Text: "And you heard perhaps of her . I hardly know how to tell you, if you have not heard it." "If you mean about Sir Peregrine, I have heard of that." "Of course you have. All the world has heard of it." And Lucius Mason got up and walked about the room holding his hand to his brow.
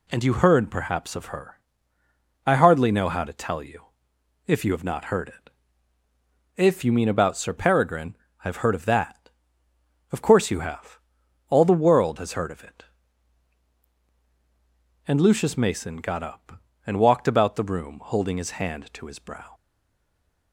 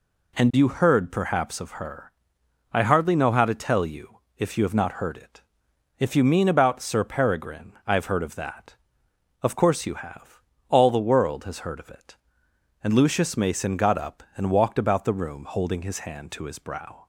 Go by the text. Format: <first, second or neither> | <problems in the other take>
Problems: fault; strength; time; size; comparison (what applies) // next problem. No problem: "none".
second | stays silent after the last word; from 19.5 s on; 1.0 s long